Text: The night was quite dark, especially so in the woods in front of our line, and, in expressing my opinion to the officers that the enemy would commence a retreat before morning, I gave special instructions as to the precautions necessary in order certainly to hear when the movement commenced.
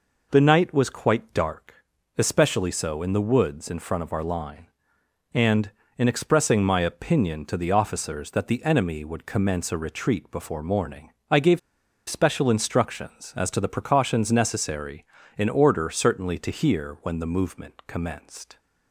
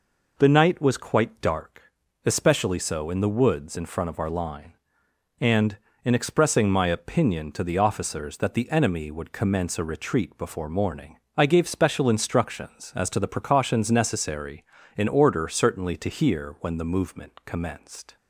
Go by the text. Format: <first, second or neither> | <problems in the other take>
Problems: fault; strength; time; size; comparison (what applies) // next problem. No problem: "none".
second | pauses between "gave" and "special"; noticeable; at 11.5 s; 0.50 s long